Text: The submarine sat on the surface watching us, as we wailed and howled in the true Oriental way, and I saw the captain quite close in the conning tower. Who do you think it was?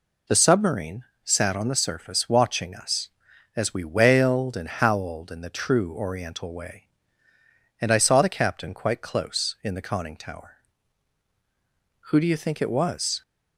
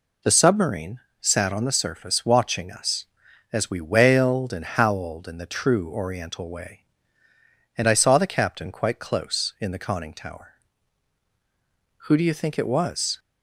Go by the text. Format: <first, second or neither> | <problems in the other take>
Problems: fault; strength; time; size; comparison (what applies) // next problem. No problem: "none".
neither | pauses between "submarine" and "sat"; slight; the same in both